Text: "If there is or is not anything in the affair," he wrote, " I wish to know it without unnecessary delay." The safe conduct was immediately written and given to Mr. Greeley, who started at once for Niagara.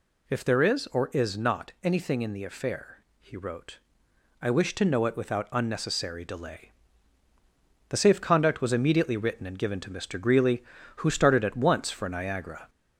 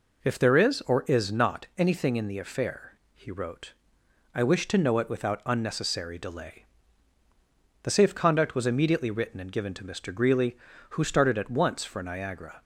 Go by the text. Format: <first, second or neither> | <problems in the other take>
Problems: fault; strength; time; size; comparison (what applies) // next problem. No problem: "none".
second | gets louder; noticeable; throughout; 4.5 dB